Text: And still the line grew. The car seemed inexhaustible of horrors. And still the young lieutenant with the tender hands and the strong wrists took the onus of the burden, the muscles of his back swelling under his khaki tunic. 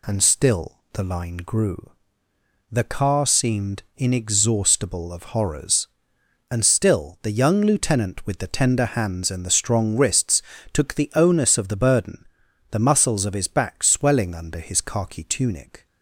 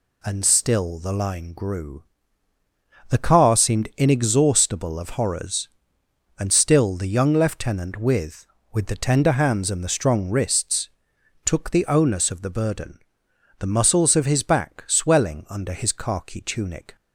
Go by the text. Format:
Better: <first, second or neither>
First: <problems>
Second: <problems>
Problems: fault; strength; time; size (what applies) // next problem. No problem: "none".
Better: first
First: pauses between "wrists" and "took"; slight; at 10.4 s; 0.30 s long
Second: says "with" twice; at 8.7 s // pauses between "wrists" and "took"; noticeable; at 10.8 s; 0.56 s long